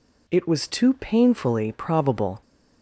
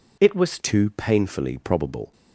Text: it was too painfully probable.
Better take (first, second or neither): first